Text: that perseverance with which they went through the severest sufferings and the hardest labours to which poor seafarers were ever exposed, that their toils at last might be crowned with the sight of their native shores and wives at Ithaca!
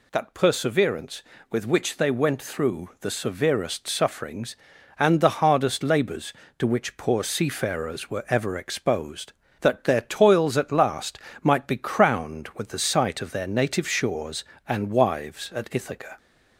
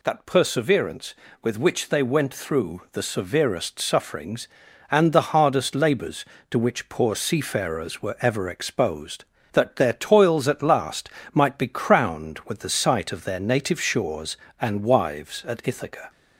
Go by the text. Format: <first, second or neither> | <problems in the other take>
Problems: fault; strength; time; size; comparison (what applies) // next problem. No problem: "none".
neither | pauses between "last" and "might"; slight; the same in both